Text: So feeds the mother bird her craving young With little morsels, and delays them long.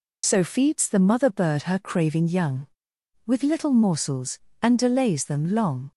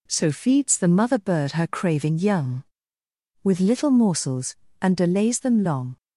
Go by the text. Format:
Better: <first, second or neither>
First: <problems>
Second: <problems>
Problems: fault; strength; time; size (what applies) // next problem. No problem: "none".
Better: second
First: loses the start of "So"; at 0.2 s; 35 ms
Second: none